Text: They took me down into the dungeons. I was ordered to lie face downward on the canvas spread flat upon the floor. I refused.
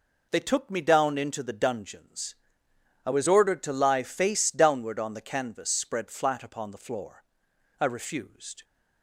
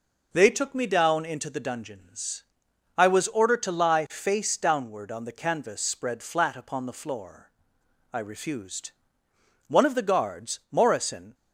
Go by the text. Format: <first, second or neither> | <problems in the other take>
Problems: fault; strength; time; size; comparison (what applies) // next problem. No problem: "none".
first | goes on to say "One of the guards Morrison"; from 9.6 s on; 1.6 s long